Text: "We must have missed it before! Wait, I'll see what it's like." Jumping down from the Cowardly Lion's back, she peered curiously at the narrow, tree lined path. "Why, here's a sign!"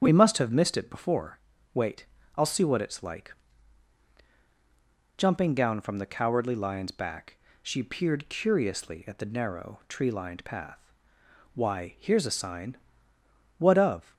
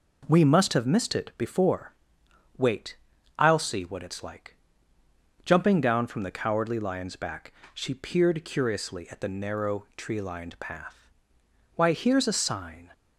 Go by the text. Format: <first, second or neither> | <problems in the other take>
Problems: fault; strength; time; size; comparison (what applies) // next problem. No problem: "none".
second | starts louder than the rest; strong; until 1.0 s; 8 dB // goes on to say "What of"; from 13.5 s on; 0.54 s long